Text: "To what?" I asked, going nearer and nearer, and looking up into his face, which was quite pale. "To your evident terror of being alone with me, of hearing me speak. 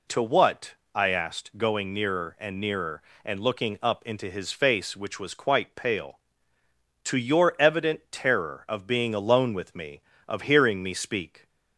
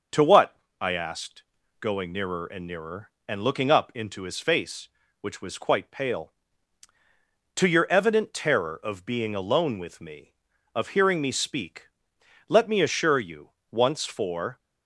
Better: first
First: none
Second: starts louder than the rest; noticeable; until 1.3 s; 6 dB // goes on to say "Let me assure you once for"; strong; from 12.4 s on; 2.1 s long

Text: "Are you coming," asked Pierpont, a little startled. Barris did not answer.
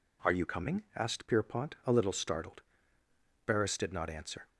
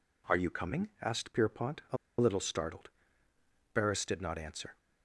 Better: first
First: none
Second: pauses between "a" and "little"; slight; at 1.9 s; 0.24 s long

